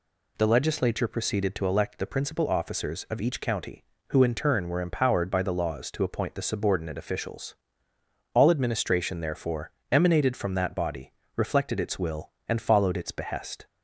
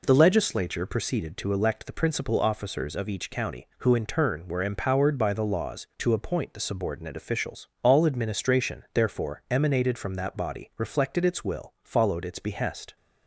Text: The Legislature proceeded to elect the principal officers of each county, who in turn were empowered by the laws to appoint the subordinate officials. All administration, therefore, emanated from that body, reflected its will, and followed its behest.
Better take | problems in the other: first | skips "and"; at 11.7 s

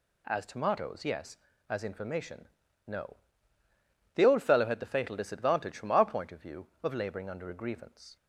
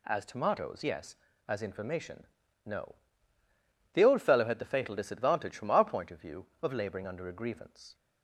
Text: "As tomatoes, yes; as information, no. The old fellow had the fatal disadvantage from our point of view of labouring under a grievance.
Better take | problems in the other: neither | none

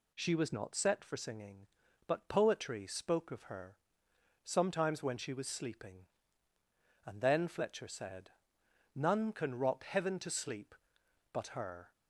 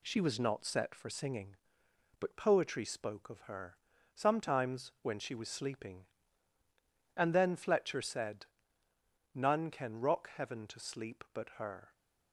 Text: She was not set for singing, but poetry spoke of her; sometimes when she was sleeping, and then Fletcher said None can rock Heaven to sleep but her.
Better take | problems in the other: first | gets quieter; slight; throughout; 3 dB // pauses between "said" and "None"; noticeable; at 8.4 s; 0.88 s long; noticeable in the first

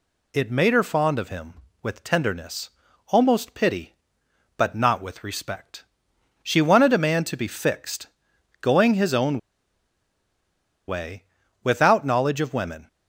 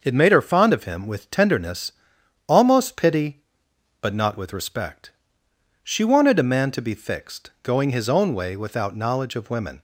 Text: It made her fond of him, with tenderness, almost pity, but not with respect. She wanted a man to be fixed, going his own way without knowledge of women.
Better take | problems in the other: second | pauses between "own" and "way"; strong; at 9.3 s; 1.4 s long // pauses between "way" and "without"; at 11.2 s; 0.40 s long

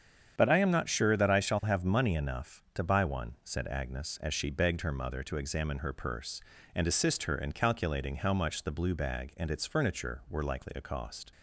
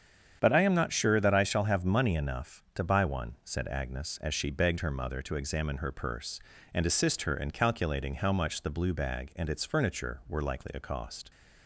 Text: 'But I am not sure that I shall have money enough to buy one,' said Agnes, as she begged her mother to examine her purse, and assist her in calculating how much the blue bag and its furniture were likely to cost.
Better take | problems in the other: neither | starts louder than the rest; strong; the same in both

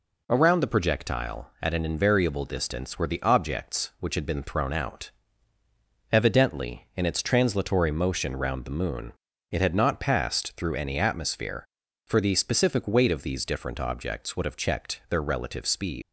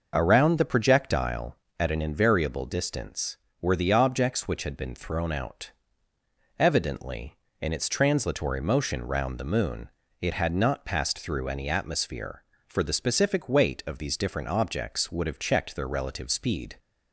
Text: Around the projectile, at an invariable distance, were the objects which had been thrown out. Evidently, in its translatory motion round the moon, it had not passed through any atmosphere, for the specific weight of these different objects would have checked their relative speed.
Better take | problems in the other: second | leaves "speed" unfinished; at 16.0 s; 125 ms

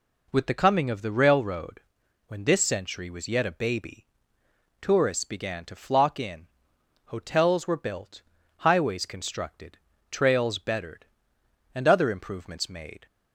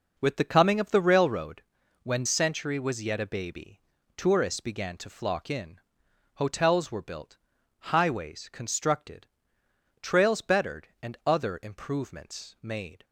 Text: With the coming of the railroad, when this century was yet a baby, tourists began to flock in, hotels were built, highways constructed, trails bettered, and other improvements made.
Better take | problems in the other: first | skips "this"; at 2.2 s

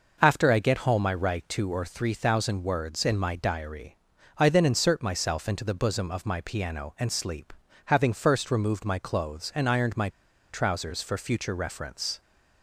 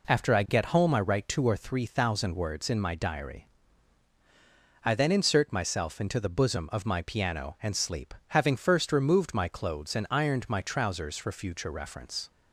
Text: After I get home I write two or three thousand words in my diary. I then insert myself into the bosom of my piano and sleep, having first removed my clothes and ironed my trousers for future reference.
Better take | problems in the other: second | pauses between "my" and "trousers"; at 10.0 s; 0.44 s long

